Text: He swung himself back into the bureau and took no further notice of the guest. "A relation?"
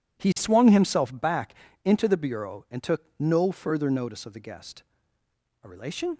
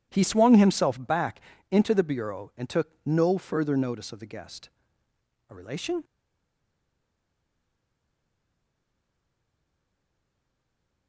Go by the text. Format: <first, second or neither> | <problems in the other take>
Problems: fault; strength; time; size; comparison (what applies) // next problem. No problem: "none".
first | pauses between "back" and "into"; slight; at 1.3 s; 0.30 s long; slight in the first // stays silent after the last word; strong; from 6.0 s on; 5.0 s long